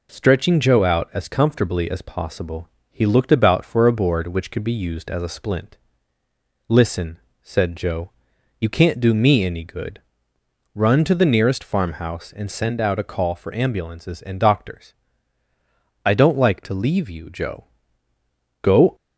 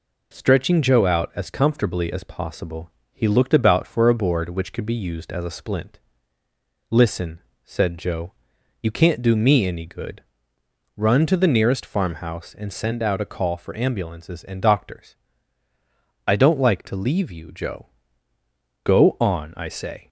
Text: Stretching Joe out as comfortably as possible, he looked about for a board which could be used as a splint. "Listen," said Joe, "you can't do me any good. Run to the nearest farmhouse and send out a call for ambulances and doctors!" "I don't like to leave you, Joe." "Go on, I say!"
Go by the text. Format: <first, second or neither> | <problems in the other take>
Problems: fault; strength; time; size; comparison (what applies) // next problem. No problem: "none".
second | stops before "on I say"; at 18.9 s